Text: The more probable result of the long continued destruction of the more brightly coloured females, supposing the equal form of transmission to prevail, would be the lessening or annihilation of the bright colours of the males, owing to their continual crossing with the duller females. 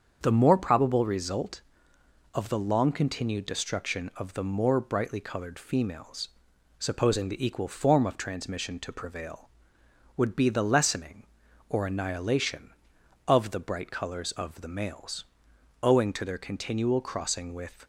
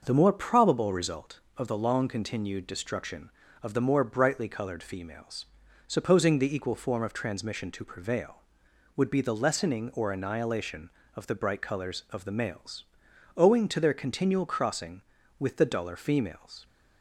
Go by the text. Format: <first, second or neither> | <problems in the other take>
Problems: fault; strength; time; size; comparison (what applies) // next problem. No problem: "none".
second | starts louder than the rest; strong; until 1.2 s; 7.5 dB; noticeable in the second // stops before "the duller females"; at 17.8 s